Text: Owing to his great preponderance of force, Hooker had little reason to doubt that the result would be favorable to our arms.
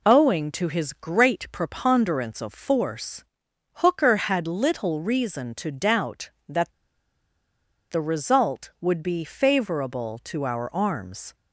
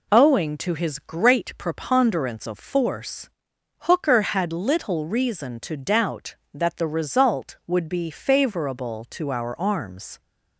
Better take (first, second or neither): second